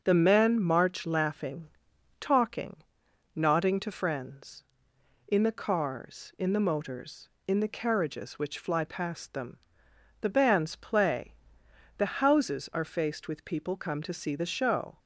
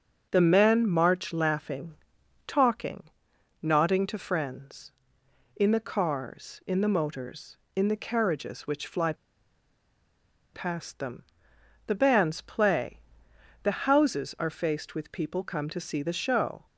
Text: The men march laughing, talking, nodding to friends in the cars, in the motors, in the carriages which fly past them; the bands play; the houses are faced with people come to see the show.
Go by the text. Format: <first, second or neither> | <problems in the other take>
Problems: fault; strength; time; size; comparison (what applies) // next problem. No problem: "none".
first | starts louder than the rest; until 1.3 s; 6 dB; also in the first // pauses between "fly" and "past"; strong; at 9.1 s; 1.3 s long